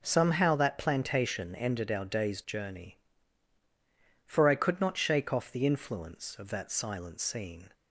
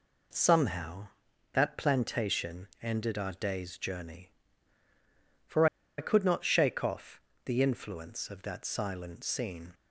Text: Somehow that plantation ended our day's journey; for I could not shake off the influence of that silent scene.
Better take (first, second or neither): first